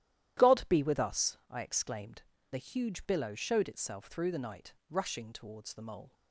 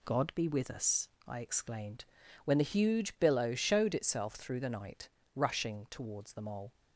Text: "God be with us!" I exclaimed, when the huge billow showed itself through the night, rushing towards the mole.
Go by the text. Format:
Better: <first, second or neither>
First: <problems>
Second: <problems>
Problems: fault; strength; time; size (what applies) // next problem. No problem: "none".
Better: second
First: starts louder than the rest; strong; until 1.5 s; 12.5 dB // skips "when"; at 2.3 s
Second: none